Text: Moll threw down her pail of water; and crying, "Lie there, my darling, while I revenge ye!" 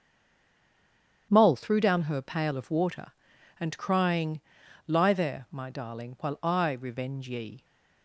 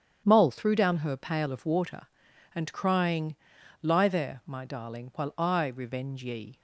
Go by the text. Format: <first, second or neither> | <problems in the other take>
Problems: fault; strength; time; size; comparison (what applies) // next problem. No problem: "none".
second | stays silent before the first word; noticeable; until 1.3 s; 1.3 s long // starts louder than the rest; strong; until 2.3 s; 9 dB; strong in the second